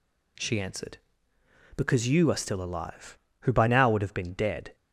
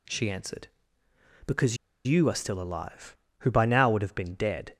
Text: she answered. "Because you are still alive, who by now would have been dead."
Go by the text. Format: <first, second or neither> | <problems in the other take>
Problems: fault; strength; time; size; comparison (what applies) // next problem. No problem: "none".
first | pauses between "Because" and "you"; slight; at 1.7 s; 0.31 s long